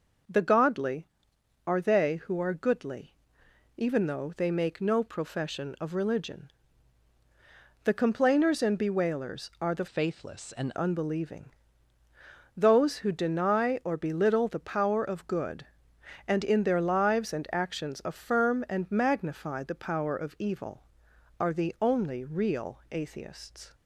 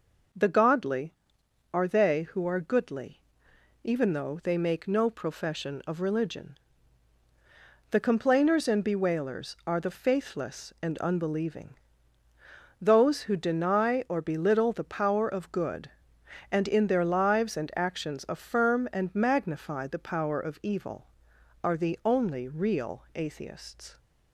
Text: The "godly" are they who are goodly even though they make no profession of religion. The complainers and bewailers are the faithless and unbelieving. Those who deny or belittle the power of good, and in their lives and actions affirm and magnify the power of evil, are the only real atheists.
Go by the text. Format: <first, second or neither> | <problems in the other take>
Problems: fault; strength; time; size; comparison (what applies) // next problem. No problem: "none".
second | pauses between "goodly" and "even"; noticeable; at 3.1 s; 0.64 s long; noticeable in the second // changes voice from "faithless" to "and"; from 9.8 to 10.7 s; 0.9 s long